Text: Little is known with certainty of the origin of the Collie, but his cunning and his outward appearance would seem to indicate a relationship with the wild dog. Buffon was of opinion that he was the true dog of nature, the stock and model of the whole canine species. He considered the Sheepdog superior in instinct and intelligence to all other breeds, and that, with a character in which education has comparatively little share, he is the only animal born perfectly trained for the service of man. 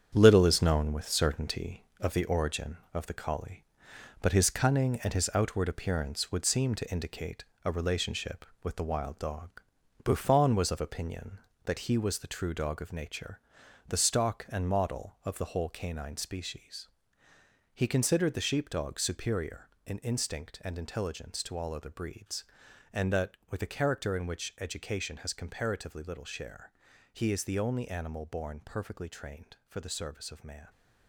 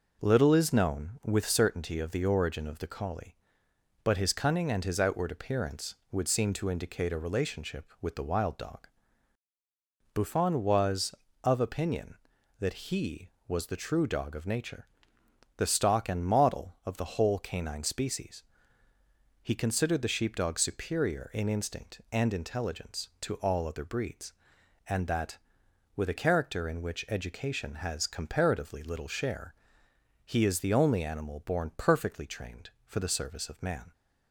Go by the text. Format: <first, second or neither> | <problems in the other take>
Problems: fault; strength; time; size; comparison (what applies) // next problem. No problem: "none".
second | gets quieter; strong; throughout; 7.5 dB // pauses between "indicate" and "a"; slight; at 7.4 s; 0.20 s long